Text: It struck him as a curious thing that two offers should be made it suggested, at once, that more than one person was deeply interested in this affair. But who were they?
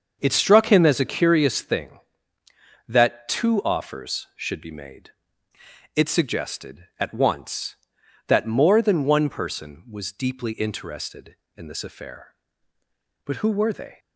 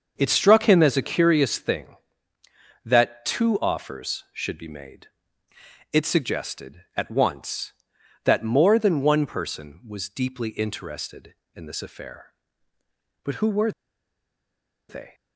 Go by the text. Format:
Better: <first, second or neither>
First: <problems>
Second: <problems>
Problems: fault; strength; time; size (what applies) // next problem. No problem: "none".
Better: first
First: starts louder than the rest; until 1.2 s; 6.5 dB // pauses between "made" and "it"; noticeable; at 5.0 s; 0.86 s long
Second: starts louder than the rest; until 1.1 s; 6.5 dB // pauses between "made" and "it"; noticeable; at 5.0 s; 0.86 s long // pauses between "were" and "they"; at 13.7 s; 1.1 s long